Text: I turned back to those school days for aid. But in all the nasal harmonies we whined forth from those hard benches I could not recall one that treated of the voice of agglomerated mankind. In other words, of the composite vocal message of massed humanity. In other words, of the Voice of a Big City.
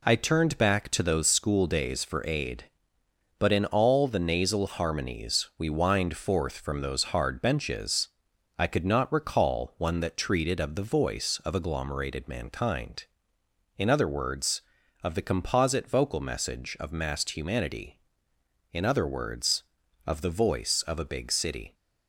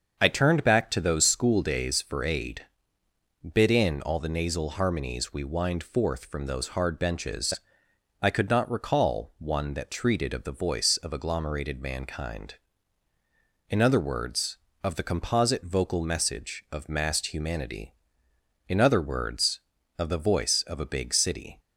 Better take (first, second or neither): first